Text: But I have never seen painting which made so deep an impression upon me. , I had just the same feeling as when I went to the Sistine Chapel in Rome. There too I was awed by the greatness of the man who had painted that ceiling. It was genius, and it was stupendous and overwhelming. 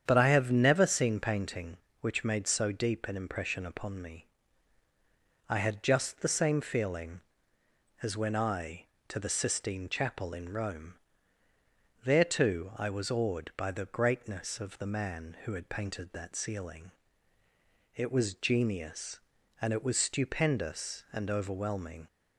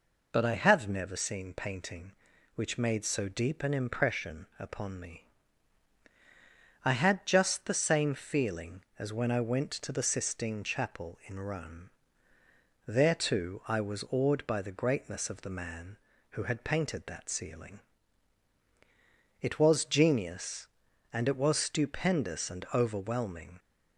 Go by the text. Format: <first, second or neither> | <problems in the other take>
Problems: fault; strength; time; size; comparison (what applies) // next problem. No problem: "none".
second | starts louder than the rest; strong; until 1.0 s; 8.5 dB // skips "went"; at 8.9 s